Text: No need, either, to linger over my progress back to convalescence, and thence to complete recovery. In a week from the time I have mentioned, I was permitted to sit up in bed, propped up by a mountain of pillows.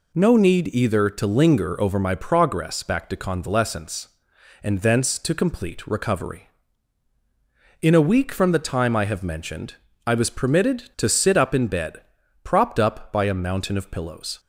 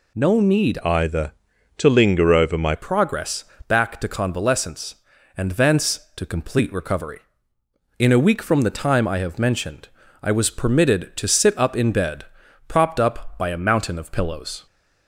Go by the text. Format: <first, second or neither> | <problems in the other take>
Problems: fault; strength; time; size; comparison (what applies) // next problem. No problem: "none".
first | changes voice from "either" to "my"; from 0.8 to 2.7 s; 1.9 s long // pauses between "progress" and "back"; slight; at 3.4 s; 0.24 s long